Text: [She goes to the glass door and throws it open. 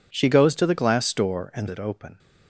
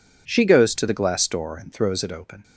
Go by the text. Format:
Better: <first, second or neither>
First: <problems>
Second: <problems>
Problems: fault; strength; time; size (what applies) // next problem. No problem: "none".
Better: second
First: skips "throws"; at 1.6 s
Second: none